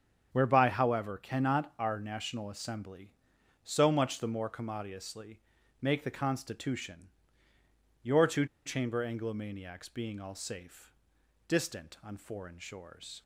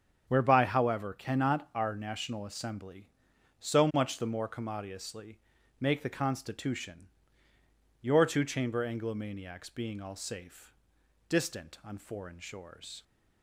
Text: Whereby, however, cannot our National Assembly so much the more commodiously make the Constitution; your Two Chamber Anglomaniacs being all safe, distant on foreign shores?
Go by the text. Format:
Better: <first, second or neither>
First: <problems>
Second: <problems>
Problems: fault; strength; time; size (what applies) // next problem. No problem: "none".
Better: second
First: starts louder than the rest; strong; until 1.3 s; 7.5 dB // pauses between "commodiously" and "make"; at 5.3 s; 0.42 s long // pauses between "Two" and "Chamber"; slight; at 8.4 s; 0.19 s long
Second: starts louder than the rest; strong; until 1.2 s; 7.5 dB // pauses between "commodiously" and "make"; at 5.3 s; 0.42 s long